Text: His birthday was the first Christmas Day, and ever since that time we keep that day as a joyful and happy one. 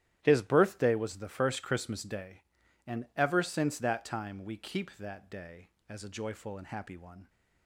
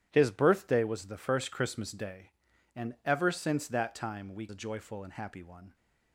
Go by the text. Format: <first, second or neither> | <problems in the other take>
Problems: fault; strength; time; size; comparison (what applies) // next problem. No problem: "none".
first | starts louder than the rest; strong; until 1.1 s; 10.5 dB; strong in the first // skips "keep that day as"; at 4.4 s